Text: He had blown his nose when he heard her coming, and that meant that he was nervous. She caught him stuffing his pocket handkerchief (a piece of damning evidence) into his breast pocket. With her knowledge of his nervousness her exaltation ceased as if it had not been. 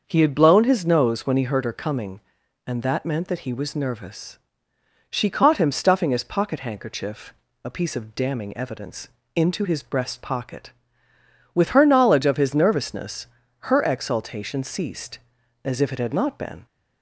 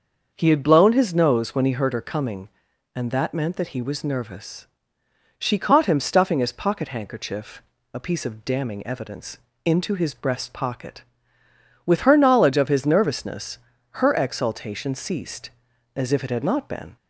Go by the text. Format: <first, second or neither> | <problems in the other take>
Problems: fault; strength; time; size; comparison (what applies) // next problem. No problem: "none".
neither | starts louder than the rest; the same in both // pauses between "nervousness" and "her"; the same in both